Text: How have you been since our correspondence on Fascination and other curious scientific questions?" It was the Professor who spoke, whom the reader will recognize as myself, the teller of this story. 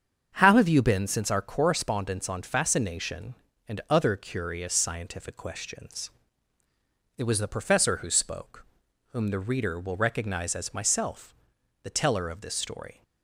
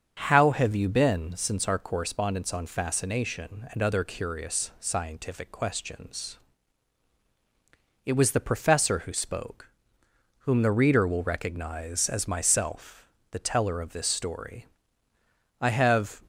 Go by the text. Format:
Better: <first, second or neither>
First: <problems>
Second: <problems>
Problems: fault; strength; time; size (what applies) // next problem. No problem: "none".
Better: first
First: starts louder than the rest; strong; until 1.3 s; 7.5 dB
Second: starts louder than the rest; strong; until 1.1 s; 7 dB // goes on to say "I have"; from 15.5 s on; 0.60 s long